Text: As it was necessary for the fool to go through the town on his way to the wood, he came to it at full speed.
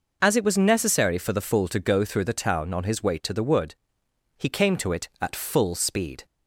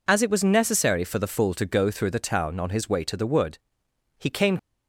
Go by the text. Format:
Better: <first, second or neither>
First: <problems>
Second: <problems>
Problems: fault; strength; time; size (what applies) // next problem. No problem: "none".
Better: first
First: none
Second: stops before "to it at full speed"; at 4.5 s